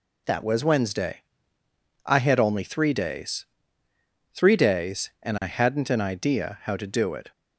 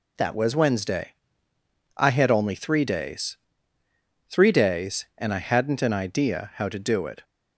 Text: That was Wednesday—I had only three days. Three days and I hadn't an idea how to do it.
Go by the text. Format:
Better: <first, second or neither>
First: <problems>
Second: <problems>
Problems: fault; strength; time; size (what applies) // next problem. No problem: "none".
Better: neither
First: none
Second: none